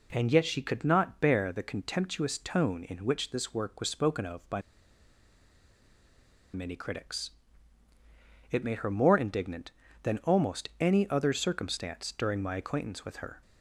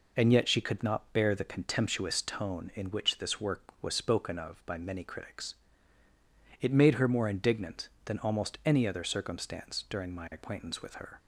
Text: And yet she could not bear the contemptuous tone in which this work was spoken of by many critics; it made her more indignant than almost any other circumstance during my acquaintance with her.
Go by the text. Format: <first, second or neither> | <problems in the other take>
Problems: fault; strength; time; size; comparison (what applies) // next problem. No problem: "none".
second | pauses between "by" and "many"; strong; at 4.6 s; 1.9 s long